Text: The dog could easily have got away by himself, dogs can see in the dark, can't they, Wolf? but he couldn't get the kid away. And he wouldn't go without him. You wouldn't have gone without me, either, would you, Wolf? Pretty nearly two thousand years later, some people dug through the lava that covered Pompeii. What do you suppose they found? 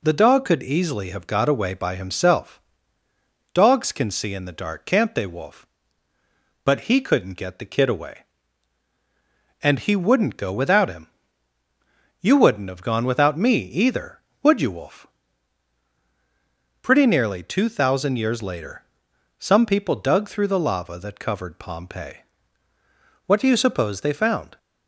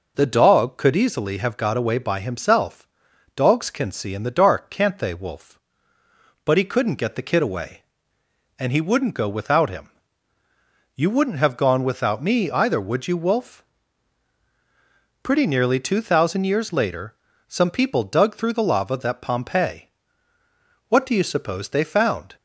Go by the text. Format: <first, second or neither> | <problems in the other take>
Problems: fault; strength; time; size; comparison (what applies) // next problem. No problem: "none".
first | skips "covered"; at 19.1 s